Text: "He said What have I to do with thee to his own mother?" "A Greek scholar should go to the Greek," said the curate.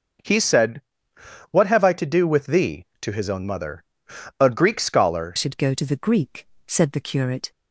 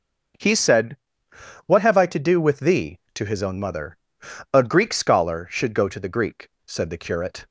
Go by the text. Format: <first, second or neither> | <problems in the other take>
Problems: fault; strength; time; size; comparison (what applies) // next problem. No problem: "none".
second | starts louder than the rest; noticeable; until 1.9 s; 6 dB; also in the second // pauses between "said" and "What"; noticeable; at 0.8 s; 0.68 s long; noticeable in the second // changes voice at "should"; from 5.3 s on; 2.2 s long